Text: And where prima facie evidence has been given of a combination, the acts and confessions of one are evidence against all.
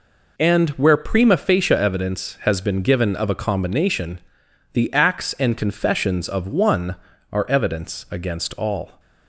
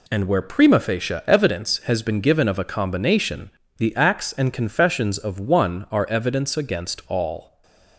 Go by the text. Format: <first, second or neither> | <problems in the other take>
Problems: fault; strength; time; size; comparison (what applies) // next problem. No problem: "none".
first | gets quieter; strong; throughout; 9.5 dB // stays silent after the last word; slight; from 7.4 s on; 0.5 s long